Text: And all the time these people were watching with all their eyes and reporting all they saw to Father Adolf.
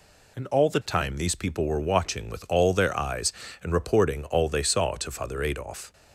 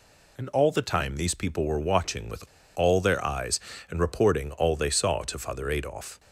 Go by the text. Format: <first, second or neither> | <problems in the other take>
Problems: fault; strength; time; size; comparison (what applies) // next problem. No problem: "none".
first | pauses between "with" and "all"; slight; at 2.4 s; 0.32 s long